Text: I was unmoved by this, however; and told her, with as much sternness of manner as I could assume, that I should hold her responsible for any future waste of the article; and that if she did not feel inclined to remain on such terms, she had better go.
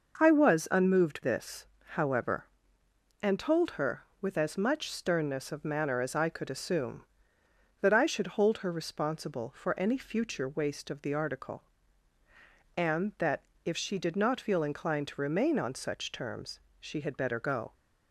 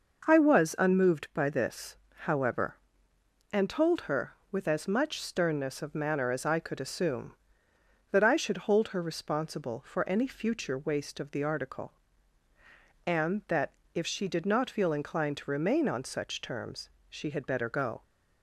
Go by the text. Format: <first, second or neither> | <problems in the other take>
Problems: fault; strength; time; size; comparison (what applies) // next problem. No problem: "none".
second | skips "by"; at 1.2 s // pauses between "that" and "if"; slight; at 13.4 s; 0.22 s long; slight in the second